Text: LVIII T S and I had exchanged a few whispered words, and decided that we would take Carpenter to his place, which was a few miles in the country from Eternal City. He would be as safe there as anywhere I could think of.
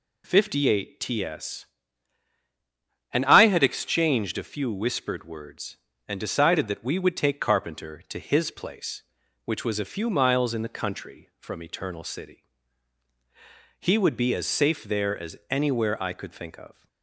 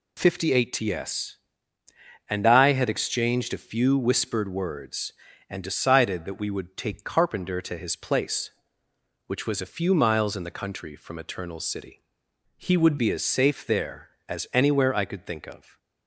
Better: first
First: none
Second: changes voice from "He" to "would"; from 12.5 to 12.9 s; 0.4 s long

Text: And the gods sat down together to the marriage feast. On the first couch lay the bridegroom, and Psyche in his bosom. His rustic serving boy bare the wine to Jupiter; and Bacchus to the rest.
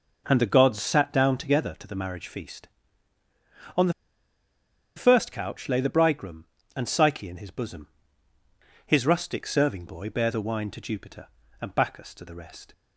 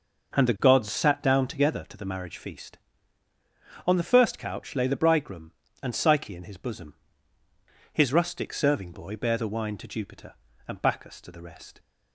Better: second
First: pauses between "the" and "first"; at 3.9 s; 1.0 s long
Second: none

